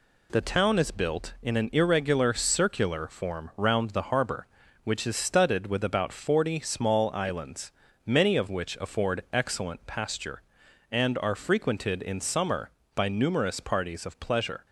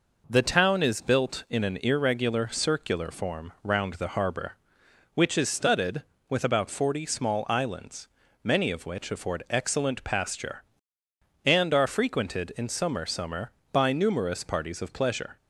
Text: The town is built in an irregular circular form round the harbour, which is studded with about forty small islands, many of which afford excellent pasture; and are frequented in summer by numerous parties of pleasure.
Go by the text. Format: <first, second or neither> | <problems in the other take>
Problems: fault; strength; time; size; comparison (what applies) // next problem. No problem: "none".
first | says "summer" twice; at 13.0 s